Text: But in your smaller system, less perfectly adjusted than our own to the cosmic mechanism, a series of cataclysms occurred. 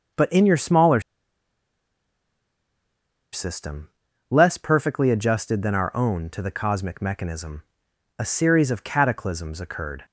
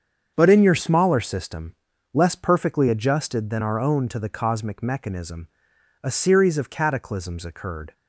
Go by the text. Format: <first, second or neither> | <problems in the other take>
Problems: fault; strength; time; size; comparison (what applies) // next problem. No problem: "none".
second | starts louder than the rest; until 3.4 s; 6.5 dB; strong in the second // pauses between "smaller" and "system"; strong; at 1.0 s; 2.3 s long